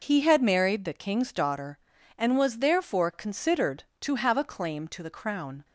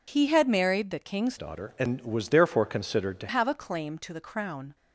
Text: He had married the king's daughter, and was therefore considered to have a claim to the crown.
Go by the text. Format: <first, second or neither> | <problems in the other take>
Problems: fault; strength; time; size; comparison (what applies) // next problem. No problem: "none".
first | changes voice from "daughter" to "to"; from 1.3 to 3.2 s; 1.9 s long